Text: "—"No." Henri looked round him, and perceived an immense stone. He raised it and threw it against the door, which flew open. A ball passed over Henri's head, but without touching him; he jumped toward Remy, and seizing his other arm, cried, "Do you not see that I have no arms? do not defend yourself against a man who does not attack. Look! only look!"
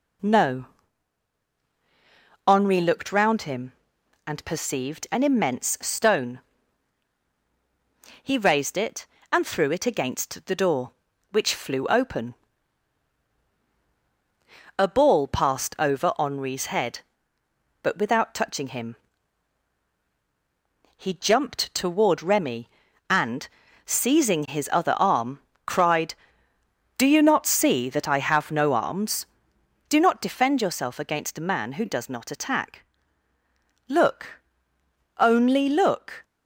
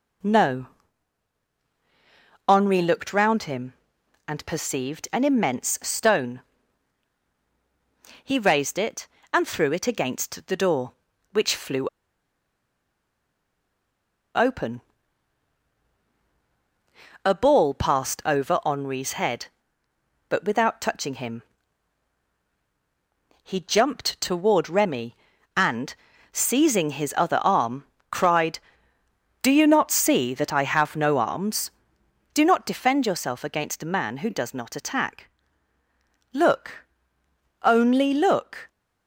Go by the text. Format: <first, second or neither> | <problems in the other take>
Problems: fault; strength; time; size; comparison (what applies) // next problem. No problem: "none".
first | pauses between "flew" and "open"; strong; at 11.8 s; 2.4 s long // pauses between "and" and "seizing"; at 25.9 s; 0.38 s long; also in the first